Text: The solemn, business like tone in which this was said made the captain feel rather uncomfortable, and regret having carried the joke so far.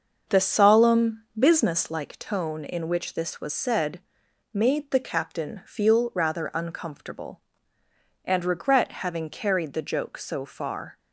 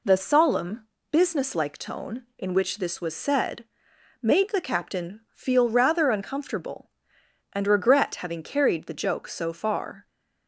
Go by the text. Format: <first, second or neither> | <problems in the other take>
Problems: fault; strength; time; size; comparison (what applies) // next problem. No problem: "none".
second | starts louder than the rest; until 1.8 s; 6.5 dB // pauses between "said" and "made"; noticeable; at 3.9 s; 0.52 s long; noticeable in the second